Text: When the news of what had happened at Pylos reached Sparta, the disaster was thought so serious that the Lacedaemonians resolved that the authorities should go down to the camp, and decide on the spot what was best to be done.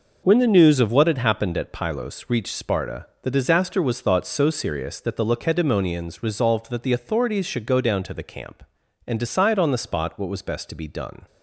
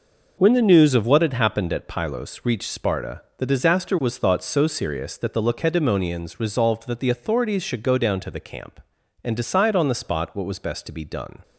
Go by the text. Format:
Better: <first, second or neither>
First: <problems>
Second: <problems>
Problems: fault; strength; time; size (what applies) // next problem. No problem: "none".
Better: neither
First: none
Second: none